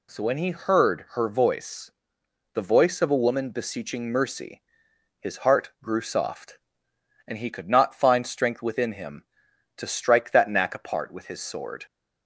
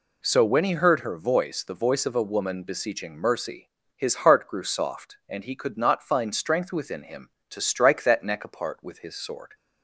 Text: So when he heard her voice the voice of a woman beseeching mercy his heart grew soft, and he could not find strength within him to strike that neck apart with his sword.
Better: second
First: pauses between "voice" and "the"; noticeable; at 1.9 s; 0.64 s long // pauses between "mercy" and "his"; noticeable; at 4.6 s; 0.58 s long // says "knack" for "neck"; at 10.4 s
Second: pauses between "mercy" and "his"; slight; at 3.7 s; 0.26 s long

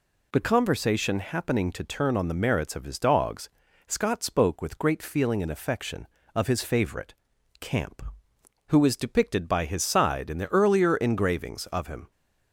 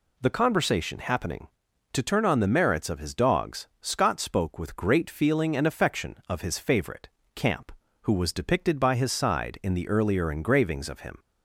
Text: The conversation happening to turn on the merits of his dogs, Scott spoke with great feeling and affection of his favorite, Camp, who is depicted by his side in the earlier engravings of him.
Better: first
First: none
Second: says "was" for "is"; at 8.1 s

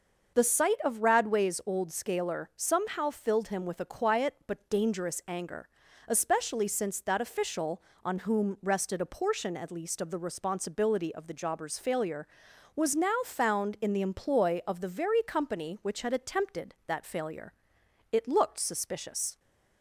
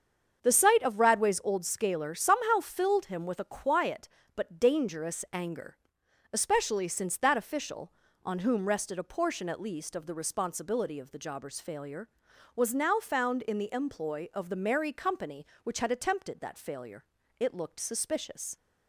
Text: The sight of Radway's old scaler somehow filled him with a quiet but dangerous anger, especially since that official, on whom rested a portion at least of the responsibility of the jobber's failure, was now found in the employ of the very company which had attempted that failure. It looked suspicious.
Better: first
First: starts louder than the rest; until 1.4 s; 6 dB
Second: starts louder than the rest; until 1.4 s; 7 dB // says "merry" for "very"; at 14.5 s

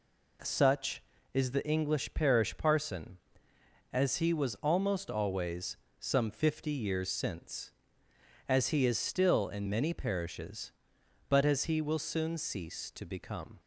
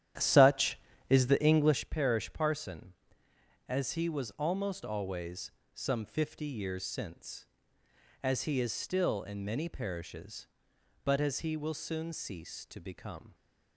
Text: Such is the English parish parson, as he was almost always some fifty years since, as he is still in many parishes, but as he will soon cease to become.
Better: first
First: pauses between "always" and "some"; slight; at 5.7 s; 0.22 s long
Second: starts louder than the rest; strong; until 1.9 s; 11 dB // pauses between "always" and "some"; slight; at 5.5 s; 0.22 s long

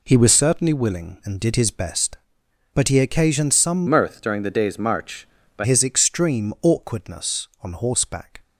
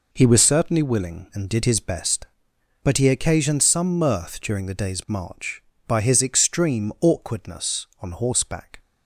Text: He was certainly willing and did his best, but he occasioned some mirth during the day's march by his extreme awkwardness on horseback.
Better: second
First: changes voice from "mirth" to "by"; from 3.8 to 5.6 s; 1.8 s long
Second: none

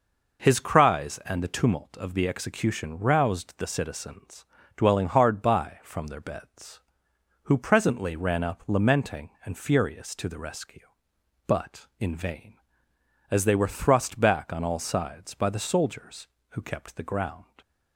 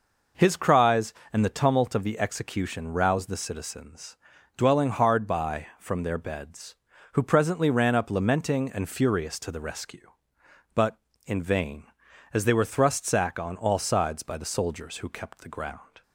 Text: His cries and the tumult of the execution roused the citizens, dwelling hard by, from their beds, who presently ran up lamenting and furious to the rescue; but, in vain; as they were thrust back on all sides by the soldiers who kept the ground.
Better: first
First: none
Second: says "sack" for "back"; at 13.0 s

